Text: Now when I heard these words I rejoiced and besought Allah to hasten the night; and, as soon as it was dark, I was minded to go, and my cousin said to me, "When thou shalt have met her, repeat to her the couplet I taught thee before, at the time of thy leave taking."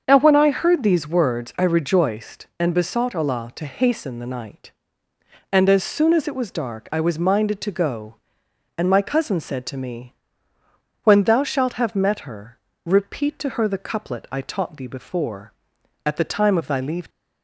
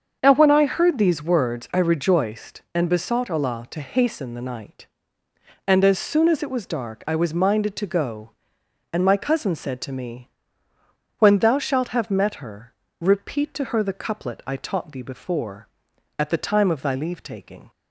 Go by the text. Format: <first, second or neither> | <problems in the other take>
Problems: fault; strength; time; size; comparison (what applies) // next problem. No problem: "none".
second | starts louder than the rest; until 1.0 s; 7 dB; also in the second // stops before "taking"; at 17.0 s